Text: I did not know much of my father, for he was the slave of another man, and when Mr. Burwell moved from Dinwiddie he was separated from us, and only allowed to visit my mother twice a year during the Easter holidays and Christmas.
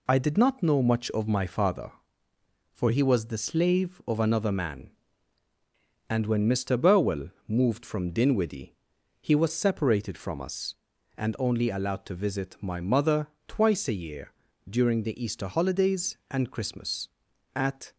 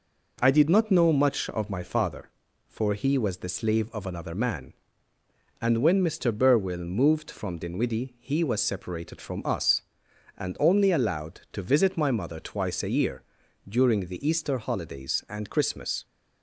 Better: second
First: pauses between "Burwell" and "moved"; slight; at 7.2 s; 0.18 s long // pauses between "Dinwiddie" and "he"; at 8.7 s; 0.44 s long // pauses between "mother" and "twice"; slight; at 13.2 s; 0.22 s long // pauses between "year" and "during"; at 14.2 s; 0.40 s long // goes on to say "At"; slight; from 17.5 s on; 0.40 s long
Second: pauses between "year" and "during"; at 13.2 s; 0.44 s long

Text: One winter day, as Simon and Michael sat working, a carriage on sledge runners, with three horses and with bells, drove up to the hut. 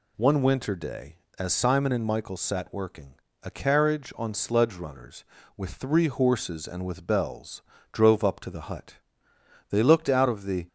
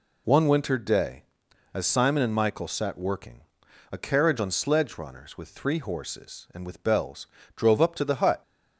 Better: second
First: goes on to say "They looked out of the"; noticeable; from 9.6 s on; 0.97 s long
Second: none

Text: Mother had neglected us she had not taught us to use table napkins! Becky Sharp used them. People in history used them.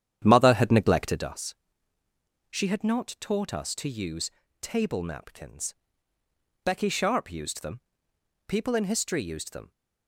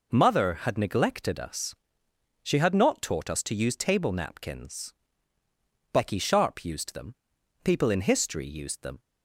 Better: second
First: starts louder than the rest; strong; until 1.4 s; 9.5 dB // pauses between "us" and "she"; noticeable; at 1.5 s; 0.94 s long // pauses between "use" and "table"; slight; at 4.2 s; 0.32 s long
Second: pauses between "us" and "she"; noticeable; at 1.7 s; 0.70 s long

